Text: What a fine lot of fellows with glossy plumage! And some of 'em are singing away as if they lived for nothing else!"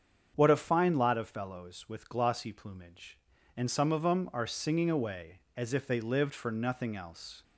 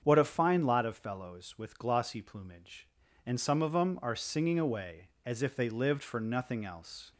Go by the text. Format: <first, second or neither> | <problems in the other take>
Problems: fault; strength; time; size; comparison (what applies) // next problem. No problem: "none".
neither | starts louder than the rest; strong; the same in both